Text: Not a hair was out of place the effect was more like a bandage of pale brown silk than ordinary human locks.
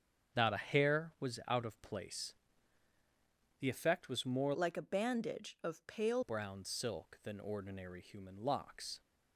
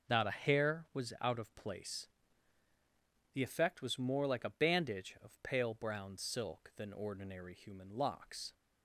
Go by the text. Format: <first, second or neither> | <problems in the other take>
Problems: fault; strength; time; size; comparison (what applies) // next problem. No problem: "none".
second | starts louder than the rest; strong; until 1.5 s; 7.5 dB // pauses between "place" and "the"; strong; at 2.3 s; 1.2 s long; strong in the second // changes voice from "like" to "pale"; from 4.5 to 6.2 s; 1.7 s long